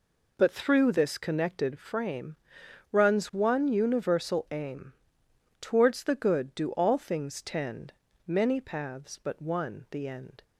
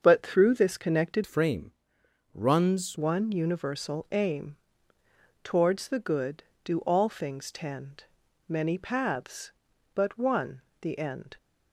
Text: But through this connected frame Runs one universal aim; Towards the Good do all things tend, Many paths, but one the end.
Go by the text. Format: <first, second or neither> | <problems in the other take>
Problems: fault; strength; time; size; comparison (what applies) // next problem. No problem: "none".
first | starts louder than the rest; until 1.0 s; 7 dB // changes voice from "frame" to "Runs"; from 1.2 to 2.9 s; 1.7 s long // pauses between "frame" and "Runs"; noticeable; at 1.7 s; 0.64 s long; noticeable in the first // pauses between "one" and "the"; slight; at 10.6 s; 0.18 s long